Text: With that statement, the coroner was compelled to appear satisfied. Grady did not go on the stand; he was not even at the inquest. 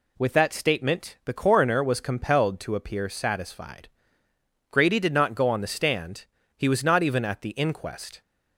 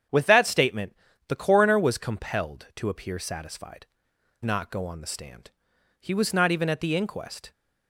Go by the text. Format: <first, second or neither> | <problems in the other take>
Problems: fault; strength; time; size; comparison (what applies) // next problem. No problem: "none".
first | starts louder than the rest; strong; until 1.4 s; 8.5 dB // skips "Grady did"; at 4.1 s